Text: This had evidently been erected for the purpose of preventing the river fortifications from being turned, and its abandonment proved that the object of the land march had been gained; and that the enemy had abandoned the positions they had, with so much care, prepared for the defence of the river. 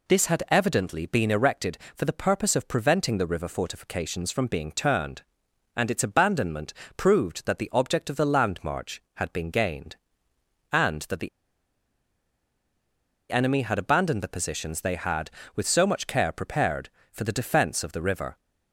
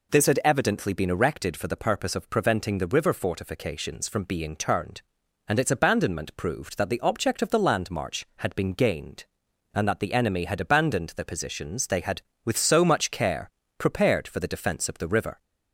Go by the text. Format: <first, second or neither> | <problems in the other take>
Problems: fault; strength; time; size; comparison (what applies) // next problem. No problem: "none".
second | pauses between "abandonment" and "proved"; slight; at 6.7 s; 0.22 s long // pauses between "the" and "enemy"; strong; at 11.2 s; 2.0 s long